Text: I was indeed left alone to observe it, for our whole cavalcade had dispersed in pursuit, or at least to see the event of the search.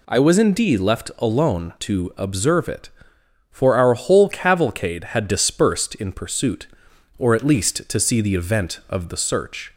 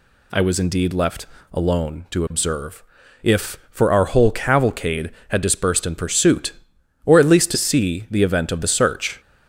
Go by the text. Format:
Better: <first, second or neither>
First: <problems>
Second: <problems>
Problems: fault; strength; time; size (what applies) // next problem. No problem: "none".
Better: first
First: none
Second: pauses between "left" and "alone"; slight; at 1.2 s; 0.28 s long // says "if" for "it"; at 3.2 s